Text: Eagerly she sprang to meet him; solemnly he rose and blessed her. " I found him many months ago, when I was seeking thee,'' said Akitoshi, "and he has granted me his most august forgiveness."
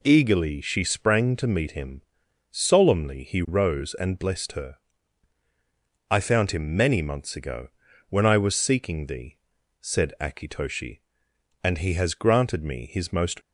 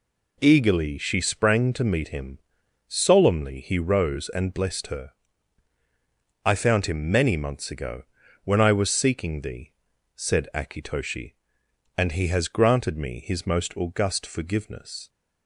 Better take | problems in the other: second | stops before "august forgiveness"; at 13.4 s

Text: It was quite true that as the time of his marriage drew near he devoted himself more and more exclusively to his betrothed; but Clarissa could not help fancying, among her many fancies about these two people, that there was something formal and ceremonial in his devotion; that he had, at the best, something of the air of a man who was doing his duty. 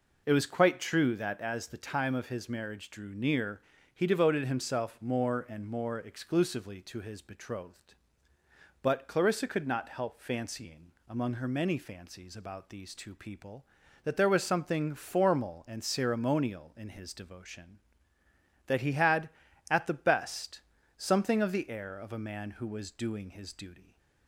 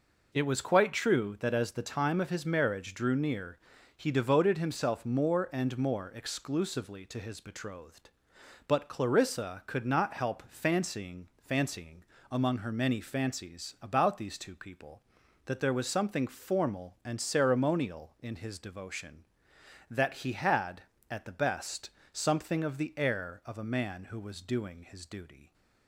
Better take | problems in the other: first | pauses between "near" and "he"; slight; at 3.5 s; 0.36 s long; slight in the first // says "fancying" twice; at 11.3 s

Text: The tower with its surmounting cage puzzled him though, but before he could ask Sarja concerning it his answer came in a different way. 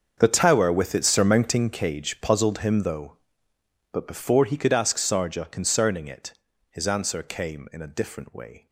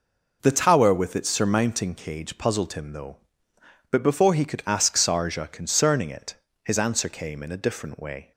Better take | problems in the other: second | gets quieter; strong; throughout; 17.5 dB // pauses between "it" and "his"; at 6.3 s; 0.38 s long; slight in the second

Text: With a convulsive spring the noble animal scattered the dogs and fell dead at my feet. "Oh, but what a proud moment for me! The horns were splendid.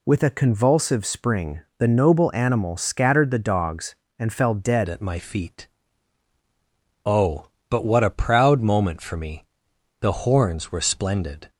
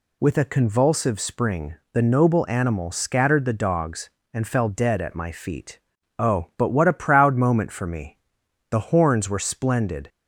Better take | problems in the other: second | pauses between "spring" and "the"; slight; at 1.6 s; 0.16 s long; slight in the second // changes voice at "at"; from 4.8 s on; 6.6 s long

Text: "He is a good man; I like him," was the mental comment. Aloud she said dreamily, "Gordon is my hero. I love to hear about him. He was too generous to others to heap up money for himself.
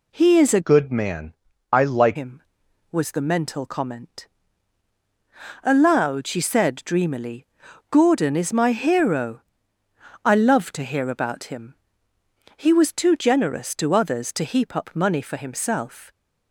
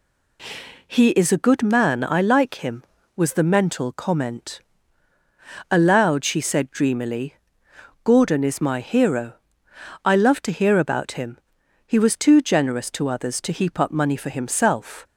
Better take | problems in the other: second | changes voice from "good" to "like"; from 0.6 to 2.1 s; 1.5 s long

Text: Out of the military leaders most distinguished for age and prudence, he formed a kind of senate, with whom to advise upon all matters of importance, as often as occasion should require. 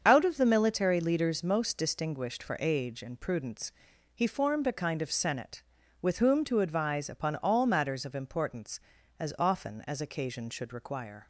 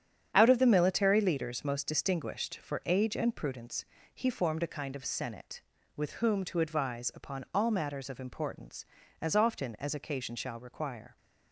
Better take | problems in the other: first | starts louder than the rest; strong; until 1.3 s; 8.5 dB; also in the first // says "shall" for "should"; at 10.3 s

